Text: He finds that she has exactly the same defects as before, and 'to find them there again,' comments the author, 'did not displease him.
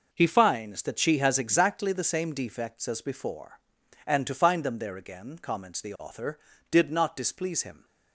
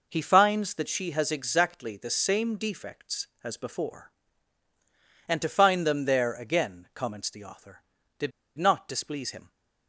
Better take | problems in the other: first | pauses between "did" and "not"; slight; at 8.3 s; 0.27 s long

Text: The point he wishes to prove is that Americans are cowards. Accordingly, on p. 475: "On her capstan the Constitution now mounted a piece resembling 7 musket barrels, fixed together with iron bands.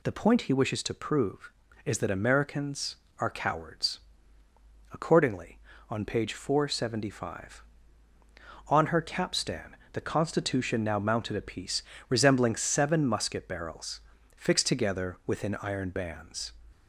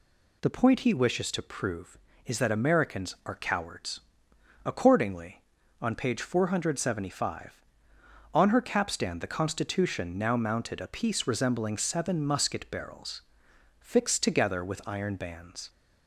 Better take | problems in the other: second | pauses between "capstan" and "the"; slight; at 9.7 s; 0.18 s long // pauses between "piece" and "resembling"; slight; at 11.8 s; 0.26 s long // says "within" for "with"; at 15.2 s

